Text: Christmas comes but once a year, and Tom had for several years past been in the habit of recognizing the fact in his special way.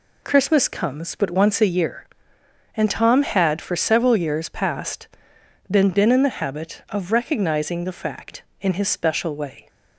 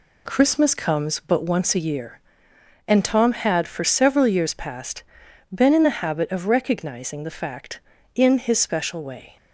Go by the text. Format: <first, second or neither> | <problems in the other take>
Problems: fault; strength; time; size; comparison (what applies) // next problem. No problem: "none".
second | pauses between "past" and "been"; noticeable; at 5.0 s; 0.60 s long; noticeable in the second // says "been" twice; at 5.8 s